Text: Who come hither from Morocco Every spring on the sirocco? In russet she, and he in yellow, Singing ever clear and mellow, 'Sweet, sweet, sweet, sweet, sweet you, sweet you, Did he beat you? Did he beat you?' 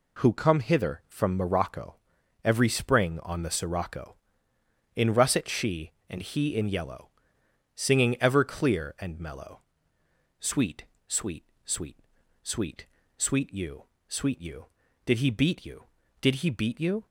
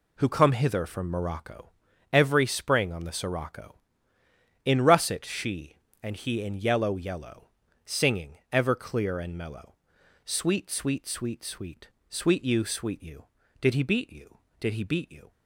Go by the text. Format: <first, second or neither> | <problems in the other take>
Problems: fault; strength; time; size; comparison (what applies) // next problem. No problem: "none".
first | pauses between "Morocco" and "Every"; at 1.7 s; 0.38 s long; noticeable in the first // says "yellow" twice; at 6.9 s